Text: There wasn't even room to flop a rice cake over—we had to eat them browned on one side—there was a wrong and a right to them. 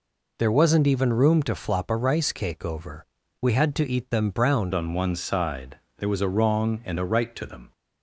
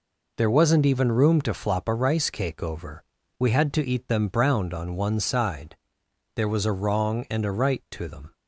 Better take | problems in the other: second | changes voice at "on"; from 4.7 s on; 3.0 s long

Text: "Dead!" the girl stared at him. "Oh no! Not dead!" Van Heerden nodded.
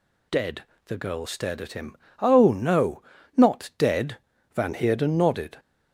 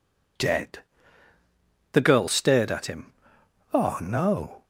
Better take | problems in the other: first | stops before "Not dead Van Heerden nodded"; at 4.6 s

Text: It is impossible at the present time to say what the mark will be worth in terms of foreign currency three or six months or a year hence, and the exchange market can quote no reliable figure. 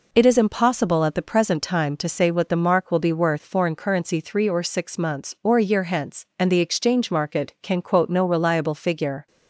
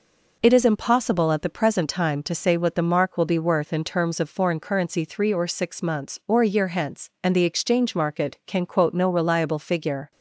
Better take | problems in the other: second | skips "in terms of"; at 3.4 s

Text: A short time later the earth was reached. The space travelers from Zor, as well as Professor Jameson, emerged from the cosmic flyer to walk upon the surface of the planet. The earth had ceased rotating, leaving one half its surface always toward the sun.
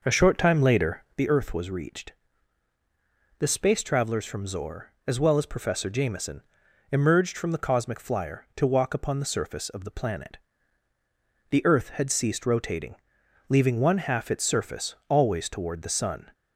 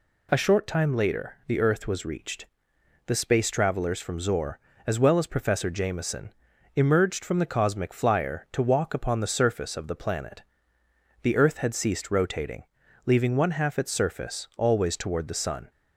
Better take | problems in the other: second | starts louder than the rest; noticeable; until 1.2 s; 5.5 dB

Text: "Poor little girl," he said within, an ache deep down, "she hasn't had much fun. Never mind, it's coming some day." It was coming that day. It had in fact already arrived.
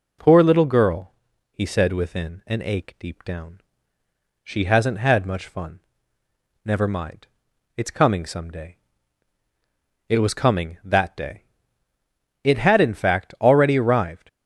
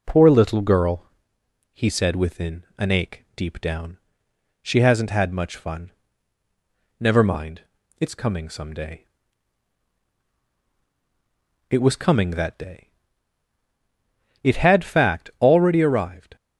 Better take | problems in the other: first | skips "in"; at 14.8 s

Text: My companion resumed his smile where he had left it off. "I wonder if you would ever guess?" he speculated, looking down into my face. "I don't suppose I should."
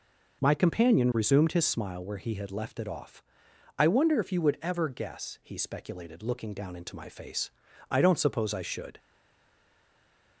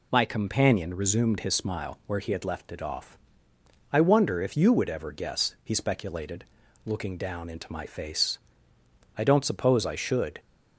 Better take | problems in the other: second | stays silent after the last word; noticeable; from 8.9 s on; 1.5 s long

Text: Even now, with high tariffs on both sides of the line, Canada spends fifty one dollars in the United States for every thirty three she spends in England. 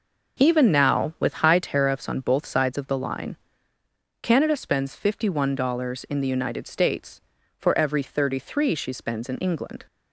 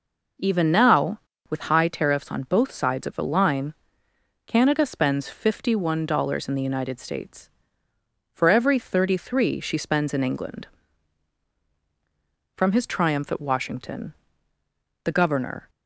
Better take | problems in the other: first | goes on to say "From his triumph at Washington the governor"; strong; from 12.5 s on; 3.1 s long

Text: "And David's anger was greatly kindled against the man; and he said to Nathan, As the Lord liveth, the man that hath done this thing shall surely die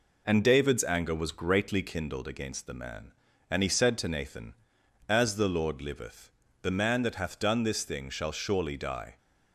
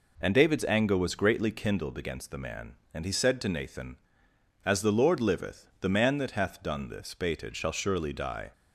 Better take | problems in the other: first | says "baited" for "thing"; at 7.1 s

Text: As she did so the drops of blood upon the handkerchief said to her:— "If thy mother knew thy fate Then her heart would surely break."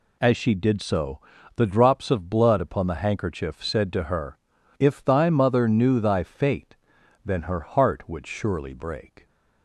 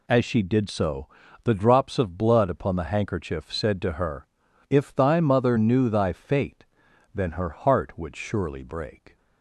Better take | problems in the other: neither | pauses between "so" and "the"; slight; the same in both // pauses between "fate" and "Then"; noticeable; the same in both

